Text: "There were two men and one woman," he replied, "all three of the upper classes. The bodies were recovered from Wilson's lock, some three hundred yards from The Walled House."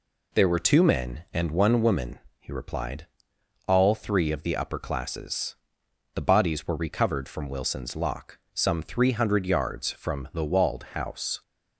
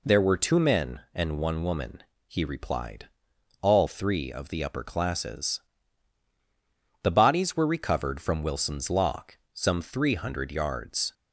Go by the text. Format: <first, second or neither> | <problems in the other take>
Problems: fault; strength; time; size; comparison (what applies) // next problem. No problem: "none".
first | stops before "from The Walled House"; at 11.1 s